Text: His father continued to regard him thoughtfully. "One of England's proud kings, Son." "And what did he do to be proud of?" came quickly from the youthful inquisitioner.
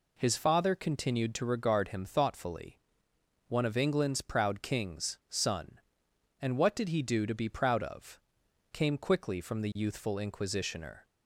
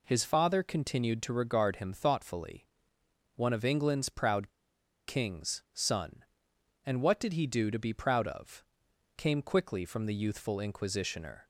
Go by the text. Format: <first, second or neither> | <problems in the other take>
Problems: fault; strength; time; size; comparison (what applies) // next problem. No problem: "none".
first | pauses between "proud" and "kings"; noticeable; at 4.5 s; 0.57 s long